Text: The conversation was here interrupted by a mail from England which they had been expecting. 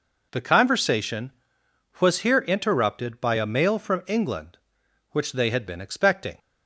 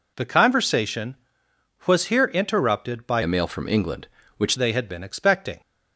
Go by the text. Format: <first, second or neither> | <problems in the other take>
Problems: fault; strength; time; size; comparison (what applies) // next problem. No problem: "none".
first | changes voice from "a" to "which"; from 3.2 to 4.5 s; 1.3 s long